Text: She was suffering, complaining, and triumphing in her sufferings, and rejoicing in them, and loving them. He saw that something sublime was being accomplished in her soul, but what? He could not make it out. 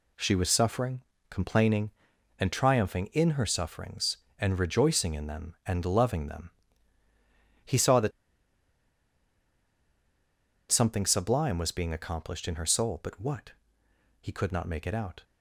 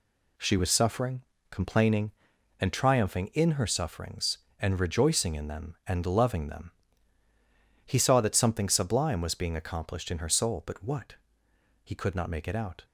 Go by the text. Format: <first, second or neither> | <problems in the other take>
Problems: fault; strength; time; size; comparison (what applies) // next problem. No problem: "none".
second | pauses between "that" and "something"; strong; at 8.1 s; 2.5 s long